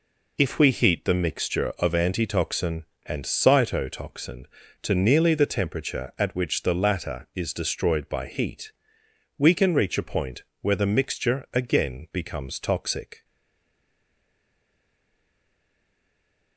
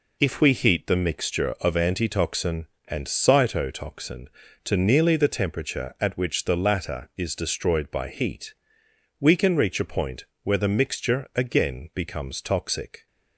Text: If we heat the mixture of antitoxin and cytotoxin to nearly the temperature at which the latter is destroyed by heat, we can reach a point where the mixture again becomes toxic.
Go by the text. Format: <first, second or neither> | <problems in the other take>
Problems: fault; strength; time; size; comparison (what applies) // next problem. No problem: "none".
second | pauses between "point" and "where"; slight; at 10.4 s; 0.18 s long; slight in the second // stays silent after the last word; strong; from 13.2 s on; 3.3 s long